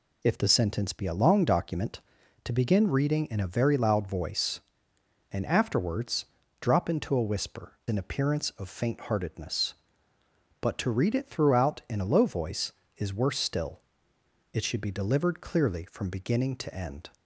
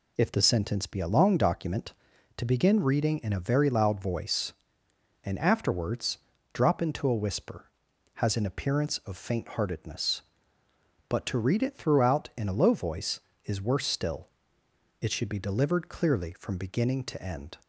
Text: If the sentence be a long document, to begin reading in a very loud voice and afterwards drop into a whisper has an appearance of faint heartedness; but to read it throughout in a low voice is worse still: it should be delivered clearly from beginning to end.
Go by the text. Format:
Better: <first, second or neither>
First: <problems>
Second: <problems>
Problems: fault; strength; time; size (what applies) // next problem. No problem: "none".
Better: second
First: pauses between "afterwards" and "drop"; slight; at 6.2 s; 0.34 s long // skips "has"; at 7.8 s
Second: pauses between "afterwards" and "drop"; slight; at 6.1 s; 0.34 s long